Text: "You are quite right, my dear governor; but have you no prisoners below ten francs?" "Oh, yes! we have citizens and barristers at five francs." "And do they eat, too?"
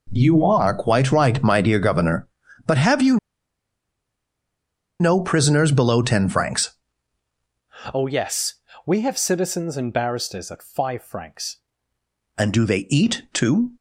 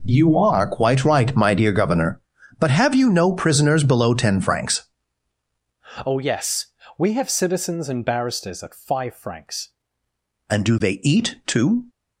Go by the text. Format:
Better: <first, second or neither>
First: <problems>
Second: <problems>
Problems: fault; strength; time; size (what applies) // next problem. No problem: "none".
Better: second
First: pauses between "you" and "no"; strong; at 3.1 s; 1.8 s long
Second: none